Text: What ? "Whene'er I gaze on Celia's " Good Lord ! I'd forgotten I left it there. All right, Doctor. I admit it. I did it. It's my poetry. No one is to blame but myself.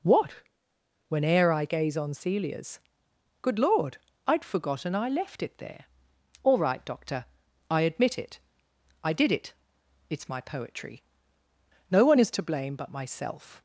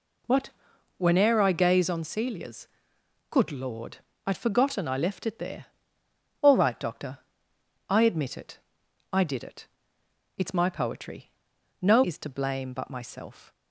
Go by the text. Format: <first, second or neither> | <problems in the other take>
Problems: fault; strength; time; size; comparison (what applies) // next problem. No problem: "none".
first | skips "one"; at 12.0 s